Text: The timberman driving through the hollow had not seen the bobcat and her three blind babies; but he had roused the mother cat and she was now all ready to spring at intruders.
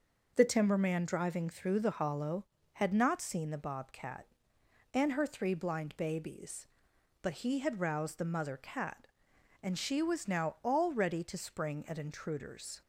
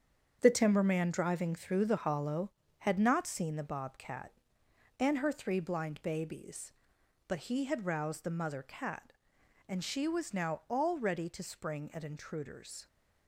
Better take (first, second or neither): first